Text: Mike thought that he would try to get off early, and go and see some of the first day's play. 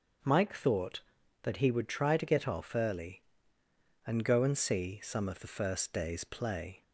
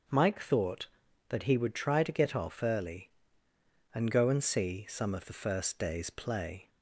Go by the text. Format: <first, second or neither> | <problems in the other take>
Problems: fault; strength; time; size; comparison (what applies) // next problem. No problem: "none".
neither | starts louder than the rest; the same in both